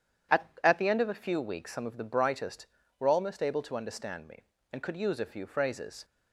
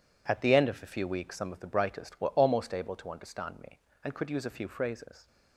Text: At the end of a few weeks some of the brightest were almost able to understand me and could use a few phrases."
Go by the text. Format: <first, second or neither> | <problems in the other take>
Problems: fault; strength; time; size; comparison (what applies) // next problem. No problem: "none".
second | says "At" twice; at 0.6 s